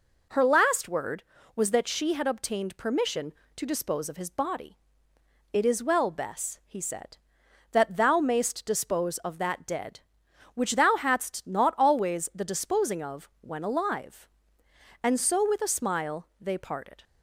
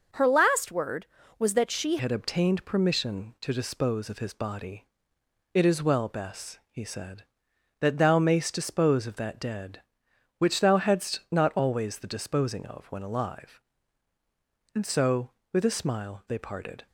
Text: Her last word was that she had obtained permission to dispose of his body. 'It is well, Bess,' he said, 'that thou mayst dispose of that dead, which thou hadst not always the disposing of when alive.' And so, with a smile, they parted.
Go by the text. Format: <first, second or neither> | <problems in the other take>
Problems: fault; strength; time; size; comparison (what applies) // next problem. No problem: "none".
first | changes voice at "had"; from 1.9 s on; 14.9 s long